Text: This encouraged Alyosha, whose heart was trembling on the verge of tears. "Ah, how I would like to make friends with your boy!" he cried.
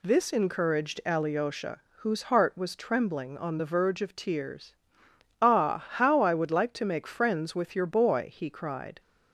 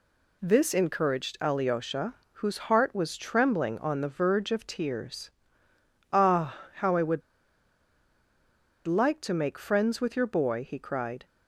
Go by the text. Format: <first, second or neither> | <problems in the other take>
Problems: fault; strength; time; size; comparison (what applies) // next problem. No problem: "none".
first | pauses between "would" and "like"; strong; at 7.2 s; 1.6 s long